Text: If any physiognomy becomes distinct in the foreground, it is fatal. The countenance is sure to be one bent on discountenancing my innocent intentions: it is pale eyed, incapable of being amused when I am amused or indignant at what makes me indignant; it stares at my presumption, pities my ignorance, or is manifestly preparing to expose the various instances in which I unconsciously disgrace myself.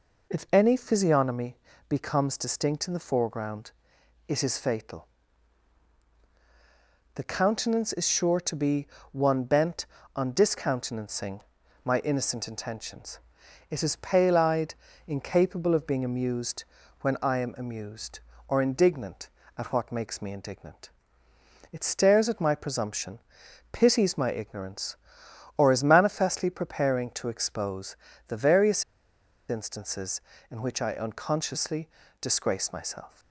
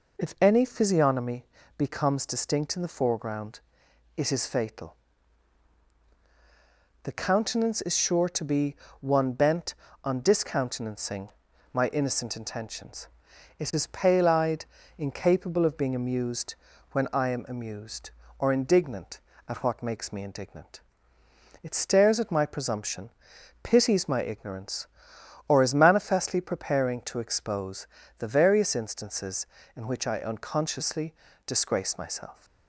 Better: second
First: pauses between "physiognomy" and "becomes"; slight; at 1.5 s; 0.32 s long // pauses between "be" and "one"; slight; at 8.8 s; 0.26 s long // pauses between "discountenancing" and "my"; at 11.3 s; 0.44 s long // pauses between "amused" and "when"; slight; at 16.6 s; 0.36 s long // pauses between "expose" and "the"; slight; at 27.9 s; 0.32 s long // pauses between "various" and "instances"; noticeable; at 28.8 s; 0.65 s long // pauses between "unconsciously" and "disgrace"; slight; at 31.8 s; 0.32 s long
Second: pauses between "physiognomy" and "becomes"; slight; at 1.4 s; 0.32 s long // pauses between "be" and "one"; slight; at 8.7 s; 0.26 s long // pauses between "discountenancing" and "my"; at 11.2 s; 0.44 s long // pauses between "amused" and "when"; slight; at 16.5 s; 0.36 s long // pauses between "expose" and "the"; slight; at 27.8 s; 0.32 s long // pauses between "unconsciously" and "disgrace"; slight; at 31.1 s; 0.32 s long

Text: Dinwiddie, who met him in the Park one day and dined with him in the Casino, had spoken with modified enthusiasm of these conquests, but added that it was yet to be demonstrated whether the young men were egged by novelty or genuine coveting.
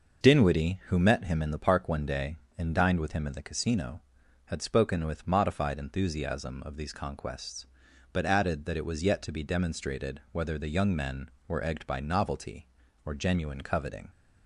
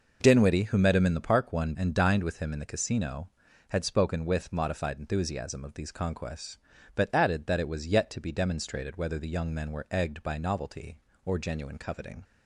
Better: first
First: none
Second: skips "day"; at 1.7 s

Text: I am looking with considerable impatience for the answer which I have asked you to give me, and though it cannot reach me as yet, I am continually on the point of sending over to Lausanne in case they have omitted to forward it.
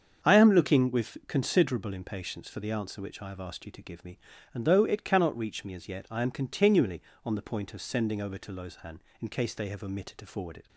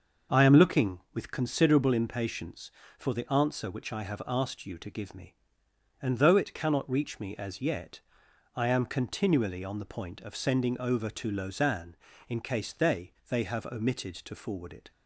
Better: first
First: starts louder than the rest; strong; until 1.3 s; 7 dB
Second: starts louder than the rest; until 1.4 s; 6 dB // says "they" twice; at 13.2 s

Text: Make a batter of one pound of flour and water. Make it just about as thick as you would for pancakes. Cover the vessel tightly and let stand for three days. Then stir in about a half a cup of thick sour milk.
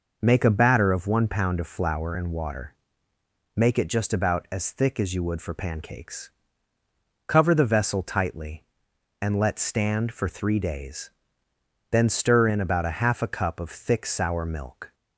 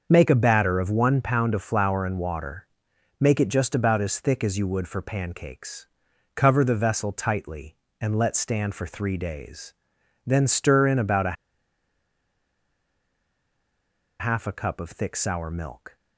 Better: first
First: none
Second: starts louder than the rest; until 1.1 s; 6.5 dB // pauses between "a" and "half"; strong; at 11.3 s; 2.8 s long

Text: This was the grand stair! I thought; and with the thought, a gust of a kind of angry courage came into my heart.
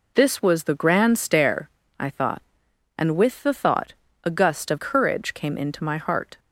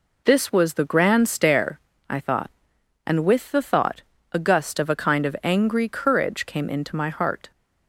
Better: second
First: skips "a kind of angry"; at 4.7 s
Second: none

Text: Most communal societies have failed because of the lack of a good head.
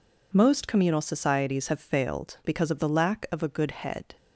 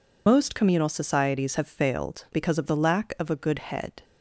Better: first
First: none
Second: loses the start of "Most"; at 0.2 s; 65 ms

